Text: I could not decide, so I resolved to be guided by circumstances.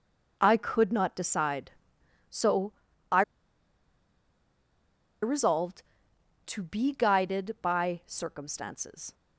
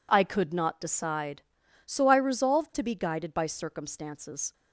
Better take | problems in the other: second | pauses between "so" and "I"; at 2.7 s; 0.38 s long // pauses between "I" and "resolved"; strong; at 3.2 s; 2.0 s long

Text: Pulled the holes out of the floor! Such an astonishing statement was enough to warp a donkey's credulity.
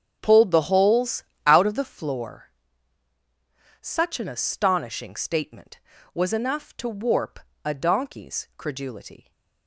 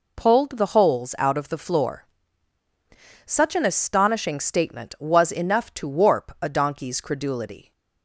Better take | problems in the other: second | starts louder than the rest; strong; until 2.1 s; 8 dB // pauses between "holes" and "out"; slight; at 1.2 s; 0.24 s long // pauses between "warp" and "a"; slight; at 7.3 s; 0.24 s long

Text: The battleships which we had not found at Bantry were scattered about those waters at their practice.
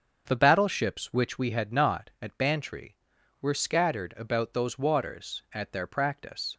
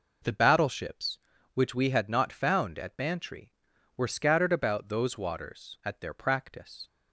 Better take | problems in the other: second | starts louder than the rest; until 1.2 s; 6.5 dB // skips "found"; at 2.1 s

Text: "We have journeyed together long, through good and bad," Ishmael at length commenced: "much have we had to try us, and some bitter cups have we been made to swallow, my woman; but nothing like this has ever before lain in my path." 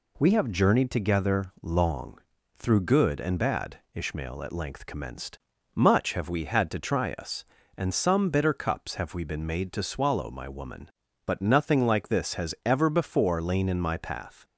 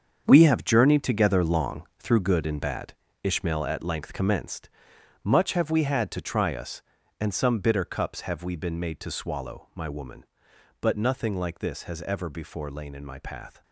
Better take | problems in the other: first | gets quieter; strong; throughout; 11 dB

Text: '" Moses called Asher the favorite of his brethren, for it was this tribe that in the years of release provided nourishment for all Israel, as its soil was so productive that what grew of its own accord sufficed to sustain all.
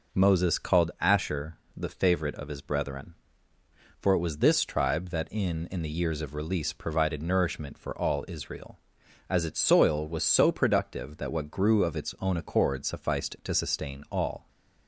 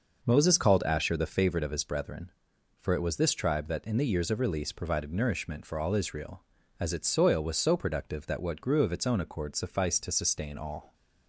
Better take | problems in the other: second | pauses between "Asher" and "the"; slight; at 1.5 s; 0.20 s long // says "in" twice; at 5.6 s

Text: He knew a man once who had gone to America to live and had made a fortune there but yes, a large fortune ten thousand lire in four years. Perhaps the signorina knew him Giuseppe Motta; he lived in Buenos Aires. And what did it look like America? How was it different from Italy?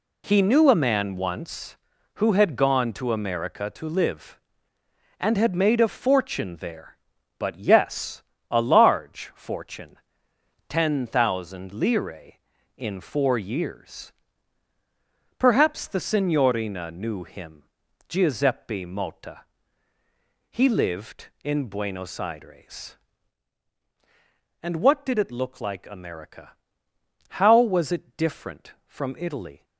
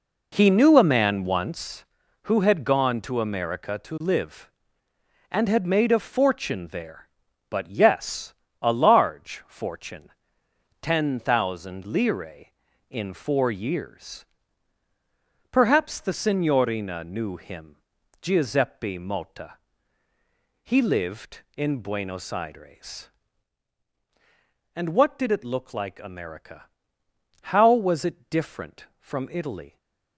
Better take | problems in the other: first | starts louder than the rest; until 1.7 s; 4 dB // pauses between "fortune" and "ten"; noticeable; at 10.0 s; 0.72 s long; noticeable in the first // pauses between "him" and "Giuseppe"; at 17.7 s; 0.44 s long; also in the first

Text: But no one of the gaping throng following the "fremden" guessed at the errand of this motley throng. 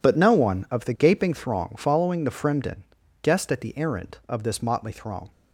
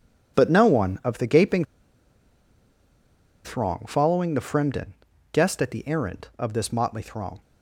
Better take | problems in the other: first | pauses between "gaping" and "throng"; strong; at 1.6 s; 1.8 s long // pauses between "fremden" and "guessed"; at 4.9 s; 0.40 s long; also in the first

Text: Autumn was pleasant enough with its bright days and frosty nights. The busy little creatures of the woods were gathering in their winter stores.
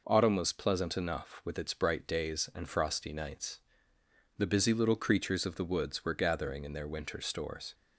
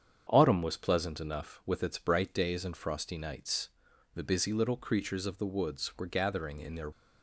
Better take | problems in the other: first | starts louder than the rest; strong; until 1.3 s; 7.5 dB // stops before "winter stores"; at 6.9 s

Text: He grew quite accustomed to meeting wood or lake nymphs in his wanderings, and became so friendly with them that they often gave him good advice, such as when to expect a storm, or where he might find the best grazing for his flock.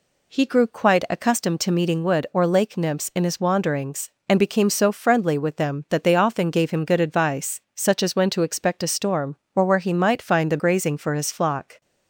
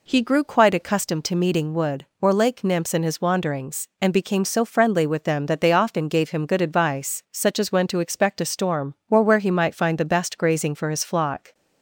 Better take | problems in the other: second | skips "best"; at 10.5 s

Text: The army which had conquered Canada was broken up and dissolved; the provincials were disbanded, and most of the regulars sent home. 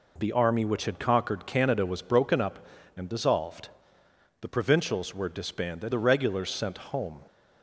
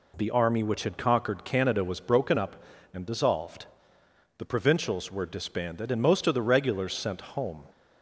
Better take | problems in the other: second | skips "and most of"; at 5.9 s

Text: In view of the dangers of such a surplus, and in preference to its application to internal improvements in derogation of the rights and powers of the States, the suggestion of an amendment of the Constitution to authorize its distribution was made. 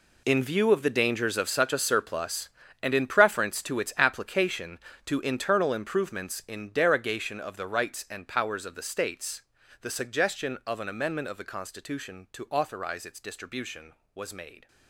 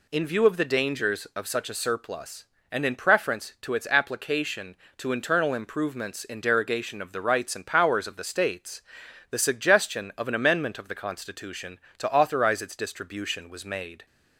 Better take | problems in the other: second | gets quieter; strong; throughout; 14 dB

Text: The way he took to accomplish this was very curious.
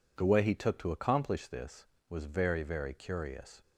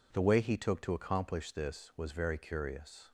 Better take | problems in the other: second | says "very" twice; at 2.6 s

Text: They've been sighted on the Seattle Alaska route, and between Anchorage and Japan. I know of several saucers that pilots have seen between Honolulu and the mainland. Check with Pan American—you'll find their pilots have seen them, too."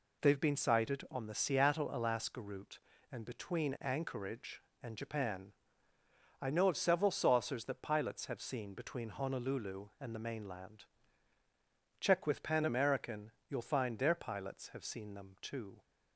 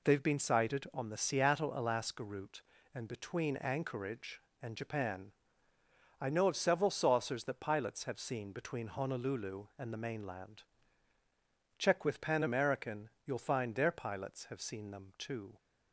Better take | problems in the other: neither | none

